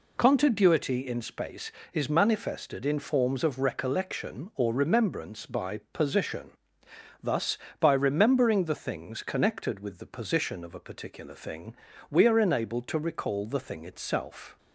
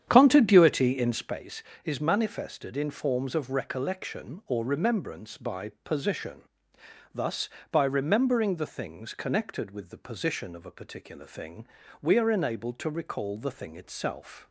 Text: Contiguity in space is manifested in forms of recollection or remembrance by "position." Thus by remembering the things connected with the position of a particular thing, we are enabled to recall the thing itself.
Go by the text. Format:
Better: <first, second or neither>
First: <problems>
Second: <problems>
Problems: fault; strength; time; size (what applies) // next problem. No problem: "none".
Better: first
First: pauses between "by" and "position"; slight; at 5.7 s; 0.16 s long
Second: starts louder than the rest; strong; until 1.4 s; 9 dB // pauses between "by" and "position"; slight; at 5.6 s; 0.16 s long